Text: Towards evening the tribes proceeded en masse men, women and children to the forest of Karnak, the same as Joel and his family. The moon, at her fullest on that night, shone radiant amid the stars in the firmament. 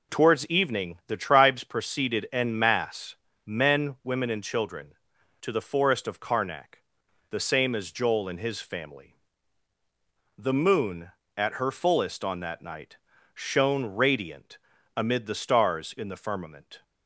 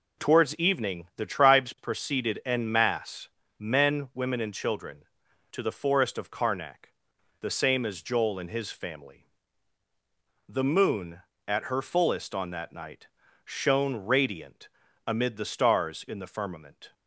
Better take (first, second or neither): neither